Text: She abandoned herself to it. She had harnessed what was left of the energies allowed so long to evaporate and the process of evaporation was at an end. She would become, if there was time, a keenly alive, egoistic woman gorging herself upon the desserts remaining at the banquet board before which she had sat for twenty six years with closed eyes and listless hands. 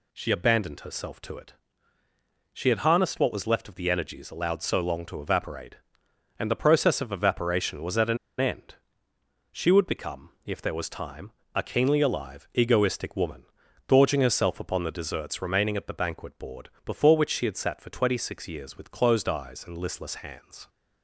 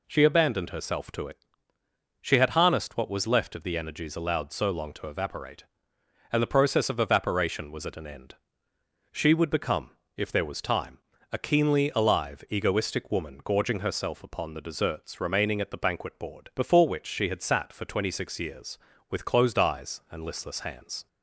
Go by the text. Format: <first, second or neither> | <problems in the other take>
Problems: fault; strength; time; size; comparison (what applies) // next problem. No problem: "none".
second | pauses between "an" and "end"; slight; at 8.1 s; 0.23 s long // pauses between "woman" and "gorging"; at 13.4 s; 0.42 s long // pauses between "board" and "before"; slight; at 16.6 s; 0.16 s long